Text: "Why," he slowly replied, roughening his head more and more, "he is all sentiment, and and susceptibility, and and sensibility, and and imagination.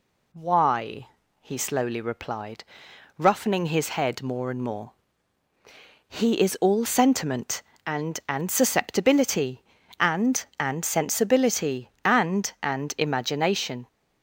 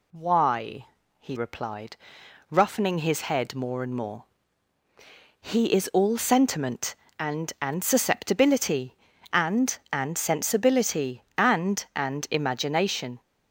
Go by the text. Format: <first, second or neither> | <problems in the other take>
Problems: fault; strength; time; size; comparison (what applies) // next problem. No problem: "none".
first | skips "slowly"; at 1.3 s